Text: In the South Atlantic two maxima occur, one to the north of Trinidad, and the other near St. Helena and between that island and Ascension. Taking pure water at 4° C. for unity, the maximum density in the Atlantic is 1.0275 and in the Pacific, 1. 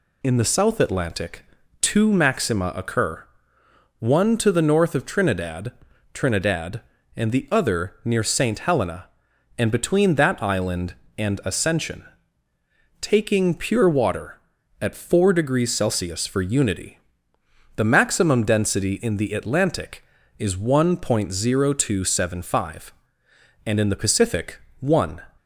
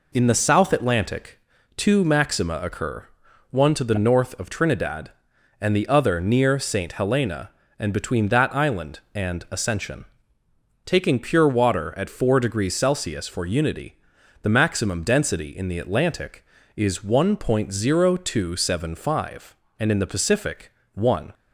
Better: second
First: pauses between "Atlantic" and "two"; slight; at 1.4 s; 0.36 s long // says "Trinidad" twice; at 6.1 s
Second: pauses between "Atlantic" and "two"; slight; at 1.3 s; 0.36 s long

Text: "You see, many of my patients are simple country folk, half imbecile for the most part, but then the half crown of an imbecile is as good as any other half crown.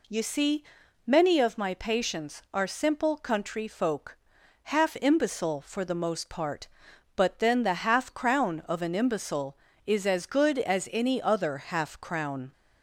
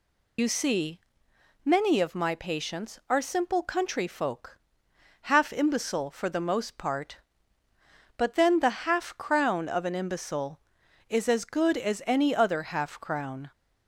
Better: first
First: none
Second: loses the start of "You"; at 0.3 s; 50 ms

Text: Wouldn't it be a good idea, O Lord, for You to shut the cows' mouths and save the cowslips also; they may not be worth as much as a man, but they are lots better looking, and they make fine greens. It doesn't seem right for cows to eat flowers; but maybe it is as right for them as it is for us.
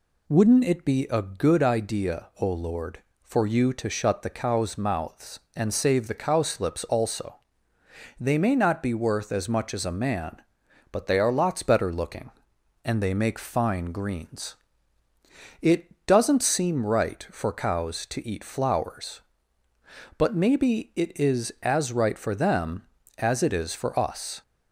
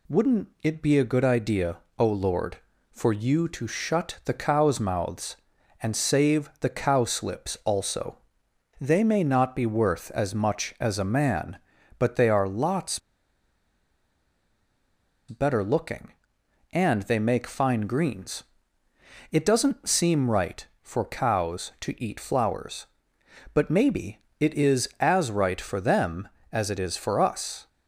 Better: first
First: none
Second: pauses between "Wouldn't" and "it"; slight; at 0.4 s; 0.16 s long // pauses between "lots" and "better"; strong; at 13.0 s; 2.2 s long // pauses between "maybe" and "it"; slight; at 24.1 s; 0.22 s long

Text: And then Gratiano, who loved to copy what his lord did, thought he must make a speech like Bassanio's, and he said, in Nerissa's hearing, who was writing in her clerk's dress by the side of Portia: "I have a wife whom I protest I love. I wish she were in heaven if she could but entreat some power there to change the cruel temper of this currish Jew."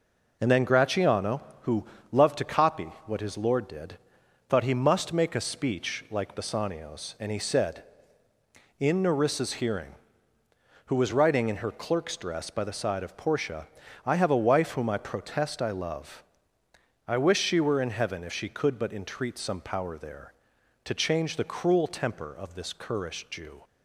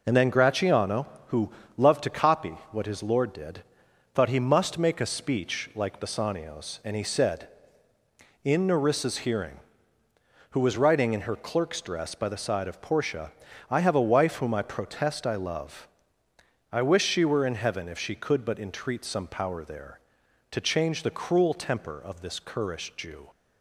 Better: neither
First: pauses between "who" and "loved"; slight; at 1.8 s; 0.28 s long // pauses between "copy" and "what"; slight; at 2.8 s; 0.16 s long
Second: pauses between "who" and "loved"; slight; at 1.4 s; 0.28 s long // pauses between "copy" and "what"; slight; at 2.5 s; 0.16 s long

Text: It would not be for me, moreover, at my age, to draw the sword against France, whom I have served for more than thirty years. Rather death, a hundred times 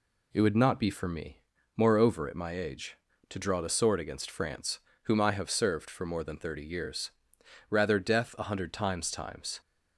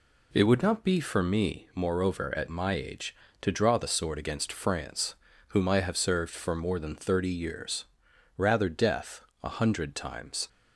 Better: second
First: says "times" twice; at 9.1 s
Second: none

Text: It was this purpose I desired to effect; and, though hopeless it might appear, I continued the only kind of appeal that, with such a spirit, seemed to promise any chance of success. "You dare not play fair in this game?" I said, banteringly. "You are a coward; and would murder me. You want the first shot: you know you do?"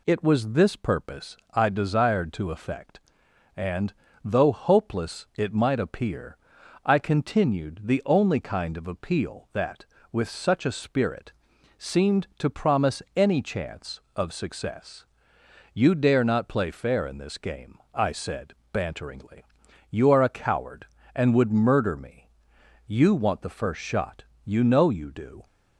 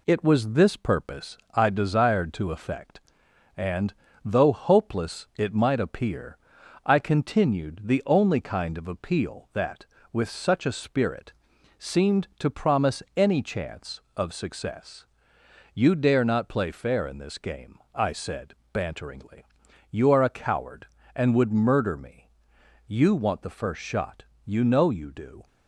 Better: first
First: pauses between "purpose" and "I"; slight; at 1.3 s; 0.16 s long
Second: gets quieter; slight; throughout; 3.5 dB // pauses between "purpose" and "I"; slight; at 1.3 s; 0.16 s long

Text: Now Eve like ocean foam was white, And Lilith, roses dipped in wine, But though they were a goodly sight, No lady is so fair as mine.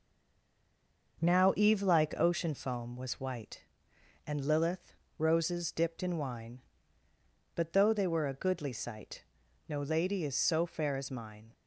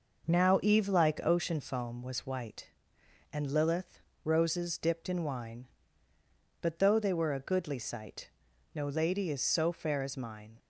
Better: second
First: stays silent before the first word; until 1.1 s; 1.1 s long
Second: none

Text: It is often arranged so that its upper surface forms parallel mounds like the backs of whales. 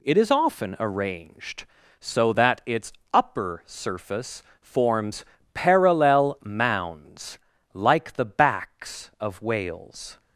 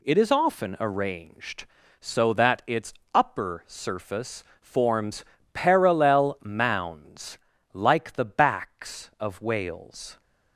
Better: neither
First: pauses between "its" and "upper"; slight; at 2.9 s; 0.20 s long // pauses between "surface" and "forms"; slight; at 4.4 s; 0.20 s long // pauses between "forms" and "parallel"; slight; at 5.2 s; 0.28 s long // pauses between "mounds" and "like"; slight; at 7.3 s; 0.36 s long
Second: pauses between "its" and "upper"; slight; at 2.9 s; 0.20 s long // pauses between "surface" and "forms"; slight; at 4.4 s; 0.18 s long // pauses between "forms" and "parallel"; slight; at 5.2 s; 0.28 s long // pauses between "mounds" and "like"; slight; at 7.3 s; 0.36 s long

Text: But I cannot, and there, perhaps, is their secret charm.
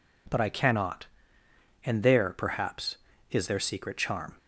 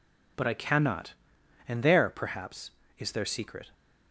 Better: first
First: none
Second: stops before "charm"; at 3.7 s

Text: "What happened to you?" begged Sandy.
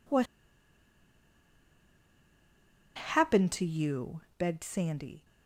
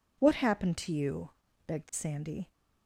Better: second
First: pauses between "What" and "happened"; strong; at 0.2 s; 2.7 s long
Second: none

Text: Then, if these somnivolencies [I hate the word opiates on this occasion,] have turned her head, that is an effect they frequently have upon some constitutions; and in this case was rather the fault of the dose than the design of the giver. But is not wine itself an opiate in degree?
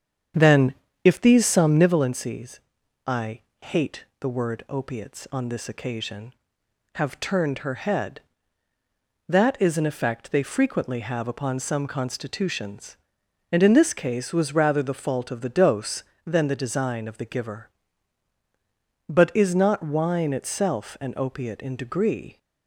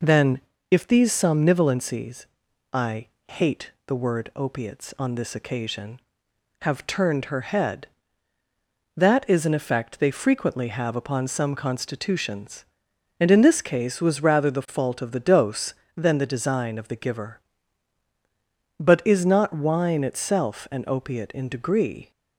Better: second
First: starts louder than the rest; strong; until 2.0 s; 8 dB // pauses between "somnivolencies" and "I"; noticeable; at 2.5 s; 0.48 s long // pauses between "I" and "hate"; slight; at 3.4 s; 0.20 s long // pauses between "hate" and "the"; slight; at 4.0 s; 0.16 s long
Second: pauses between "somnivolencies" and "I"; noticeable; at 2.2 s; 0.48 s long // pauses between "I" and "hate"; slight; at 3.0 s; 0.20 s long // pauses between "hate" and "the"; slight; at 3.6 s; 0.16 s long

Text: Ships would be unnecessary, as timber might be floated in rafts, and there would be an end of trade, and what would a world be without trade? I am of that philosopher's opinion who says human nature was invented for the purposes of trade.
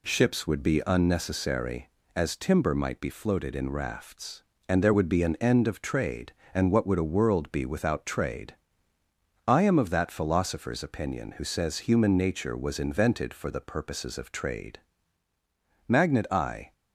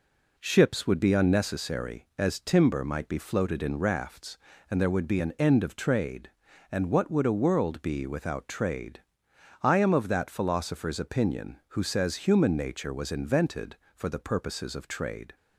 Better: second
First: goes on to say "Magnet I"; noticeable; from 15.8 s on; 0.86 s long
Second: none

